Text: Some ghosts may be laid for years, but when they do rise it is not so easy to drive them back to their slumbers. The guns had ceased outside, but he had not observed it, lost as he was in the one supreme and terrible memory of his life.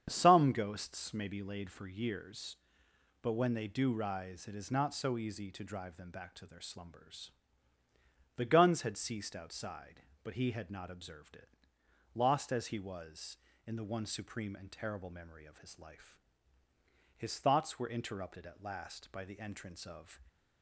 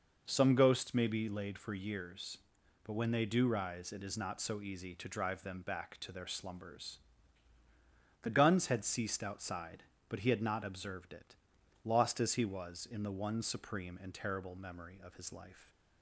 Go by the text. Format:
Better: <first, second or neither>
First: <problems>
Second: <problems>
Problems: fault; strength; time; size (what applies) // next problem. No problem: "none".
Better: second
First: starts louder than the rest; strong; until 1.0 s; 8 dB // goes on to say "His thoughts were interrupted at last by the entrance of"; strong; from 17.1 s on; 3.0 s long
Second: none